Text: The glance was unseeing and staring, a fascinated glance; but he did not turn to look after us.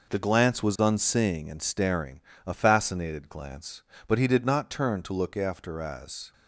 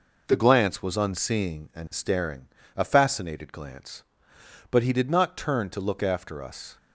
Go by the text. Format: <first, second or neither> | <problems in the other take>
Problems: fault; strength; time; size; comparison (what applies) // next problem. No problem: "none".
second | says "as" for "us"; at 5.7 s